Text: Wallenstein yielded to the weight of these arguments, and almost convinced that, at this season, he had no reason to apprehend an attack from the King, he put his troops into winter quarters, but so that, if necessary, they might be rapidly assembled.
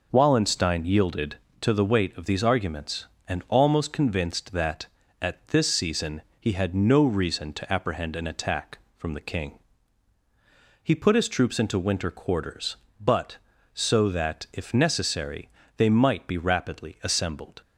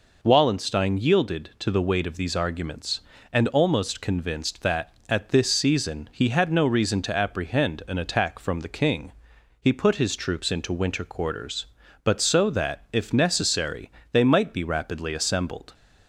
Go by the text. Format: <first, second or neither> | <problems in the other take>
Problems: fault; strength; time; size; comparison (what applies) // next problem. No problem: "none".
neither | none